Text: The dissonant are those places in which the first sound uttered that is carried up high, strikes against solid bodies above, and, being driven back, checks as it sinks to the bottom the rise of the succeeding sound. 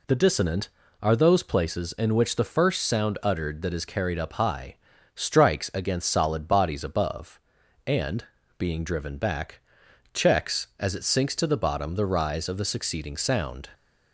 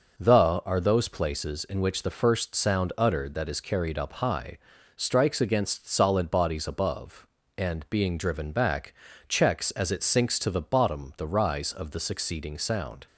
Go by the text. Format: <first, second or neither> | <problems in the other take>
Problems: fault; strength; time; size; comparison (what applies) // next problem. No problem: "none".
first | skips "dissonant"; at 0.6 s